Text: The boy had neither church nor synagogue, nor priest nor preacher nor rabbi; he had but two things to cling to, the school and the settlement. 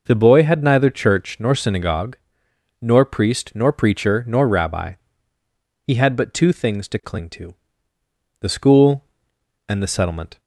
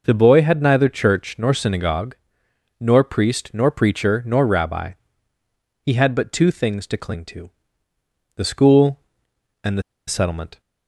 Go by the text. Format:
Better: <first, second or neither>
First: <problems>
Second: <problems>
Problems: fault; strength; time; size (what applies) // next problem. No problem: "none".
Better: first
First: none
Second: pauses between "the" and "settlement"; slight; at 9.8 s; 0.26 s long